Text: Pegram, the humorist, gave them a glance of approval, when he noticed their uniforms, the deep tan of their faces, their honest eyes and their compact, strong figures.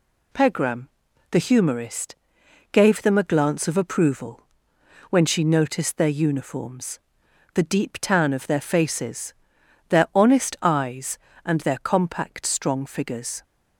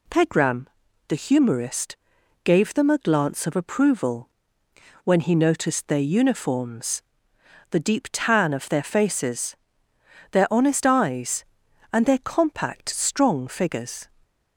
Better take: second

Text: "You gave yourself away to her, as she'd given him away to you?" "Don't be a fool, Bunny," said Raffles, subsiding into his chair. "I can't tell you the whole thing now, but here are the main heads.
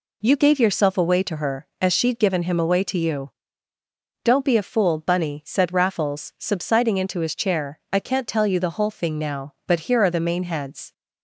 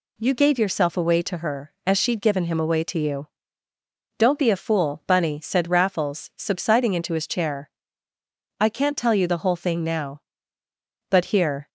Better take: first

